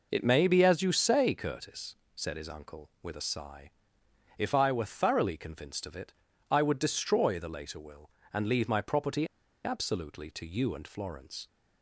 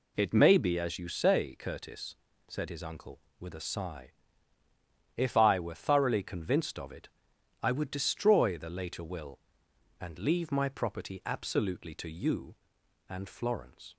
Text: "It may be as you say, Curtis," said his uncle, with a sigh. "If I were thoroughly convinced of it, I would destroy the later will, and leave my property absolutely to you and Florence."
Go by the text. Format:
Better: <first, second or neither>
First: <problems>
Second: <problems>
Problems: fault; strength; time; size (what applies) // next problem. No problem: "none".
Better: second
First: pauses between "property" and "absolutely"; at 9.2 s; 0.39 s long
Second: none